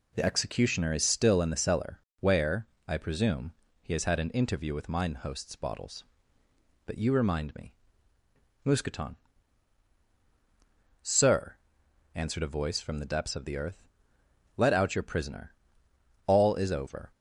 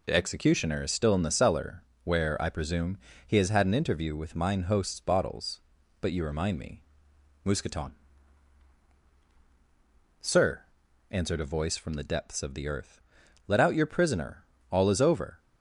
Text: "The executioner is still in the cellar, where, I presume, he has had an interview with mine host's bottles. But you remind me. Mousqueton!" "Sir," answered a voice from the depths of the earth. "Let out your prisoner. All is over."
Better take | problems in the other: neither | none

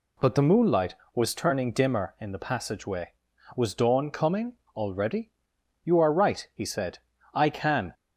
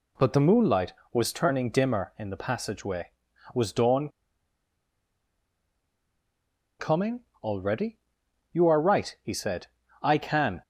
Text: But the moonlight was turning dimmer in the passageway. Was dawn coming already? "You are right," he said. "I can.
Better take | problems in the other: first | pauses between "dawn" and "coming"; strong; at 4.0 s; 2.7 s long // pauses between "coming" and "already"; slight; at 7.2 s; 0.22 s long; slight in the first

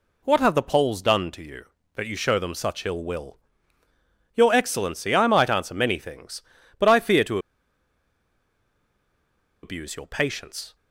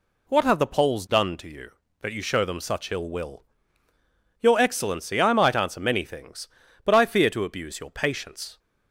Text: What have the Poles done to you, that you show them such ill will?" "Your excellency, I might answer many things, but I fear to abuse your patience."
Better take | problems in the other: second | pauses between "to" and "abuse"; strong; at 7.3 s; 2.2 s long

